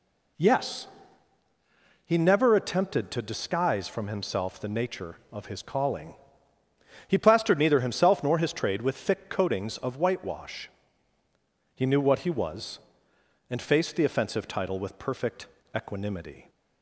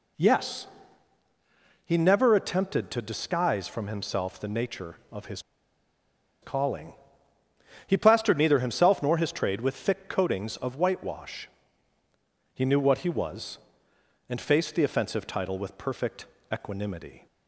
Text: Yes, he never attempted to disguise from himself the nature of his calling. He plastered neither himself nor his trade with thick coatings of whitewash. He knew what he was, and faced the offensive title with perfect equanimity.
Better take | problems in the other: first | pauses between "his" and "calling"; at 5.4 s; 1.0 s long // pauses between "perfect" and "equanimity"; slight; at 16.2 s; 0.26 s long; slight in the first

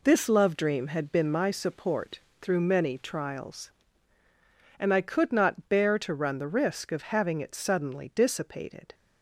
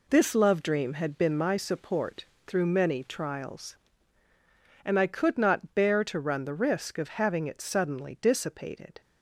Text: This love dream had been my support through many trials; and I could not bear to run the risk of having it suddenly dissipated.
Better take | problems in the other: neither | pauses between "support" and "through"; slight; the same in both

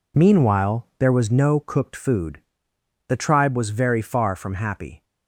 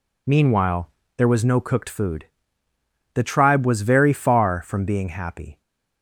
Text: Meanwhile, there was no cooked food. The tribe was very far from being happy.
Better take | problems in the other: second | skips "being"; at 4.5 s

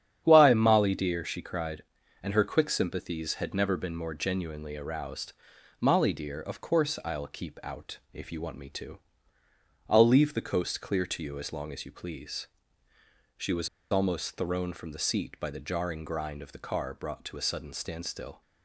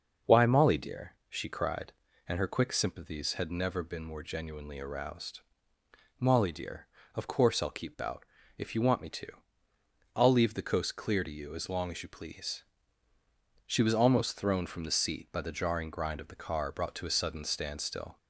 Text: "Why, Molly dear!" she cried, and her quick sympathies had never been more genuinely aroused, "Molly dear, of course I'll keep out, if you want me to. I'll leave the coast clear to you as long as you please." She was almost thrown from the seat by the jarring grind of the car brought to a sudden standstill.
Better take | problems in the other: second | starts louder than the rest; strong; until 1.2 s; 9 dB; noticeable in the second // pauses between "was" and "almost"; slight; at 13.6 s; 0.22 s long

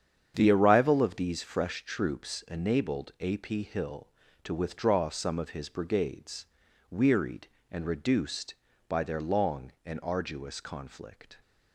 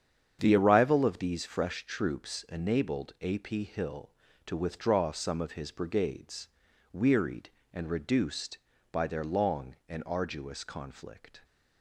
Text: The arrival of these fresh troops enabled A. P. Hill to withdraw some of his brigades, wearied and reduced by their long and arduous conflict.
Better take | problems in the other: neither | starts louder than the rest; strong; the same in both

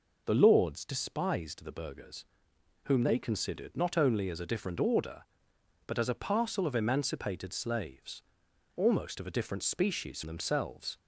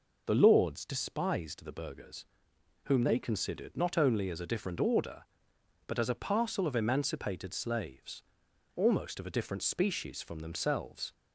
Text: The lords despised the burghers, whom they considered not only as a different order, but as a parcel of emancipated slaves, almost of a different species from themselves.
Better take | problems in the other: second | skips "from"; at 10.2 s

